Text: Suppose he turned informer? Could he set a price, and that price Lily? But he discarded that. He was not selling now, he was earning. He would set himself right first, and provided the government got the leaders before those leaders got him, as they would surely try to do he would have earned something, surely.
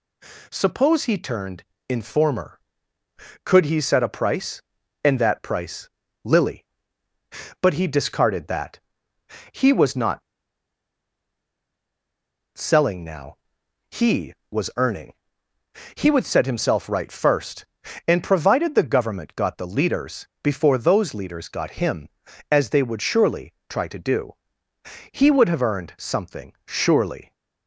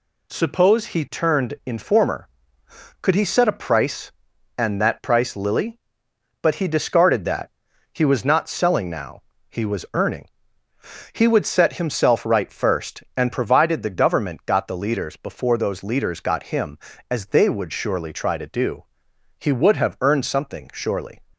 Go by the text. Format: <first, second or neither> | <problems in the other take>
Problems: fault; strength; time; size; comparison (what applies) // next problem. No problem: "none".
second | pauses between "turned" and "informer"; slight; at 1.6 s; 0.28 s long // pauses between "price" and "Lily"; slight; at 5.9 s; 0.34 s long // pauses between "not" and "selling"; strong; at 10.2 s; 2.3 s long // pauses between "do" and "he"; noticeable; at 24.3 s; 0.78 s long; noticeable in the second